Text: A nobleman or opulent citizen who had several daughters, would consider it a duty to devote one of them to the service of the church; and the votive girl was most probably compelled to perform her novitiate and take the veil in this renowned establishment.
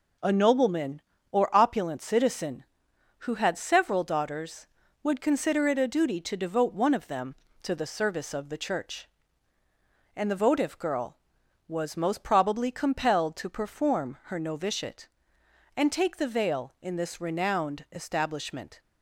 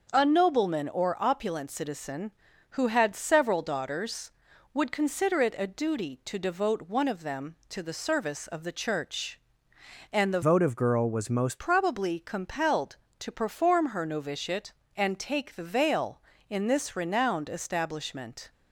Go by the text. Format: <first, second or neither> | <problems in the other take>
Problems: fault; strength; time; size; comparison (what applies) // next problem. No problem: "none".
first | starts louder than the rest; until 1.1 s; 6.5 dB // changes voice from "votive" to "most"; from 10.4 to 11.5 s; 1.1 s long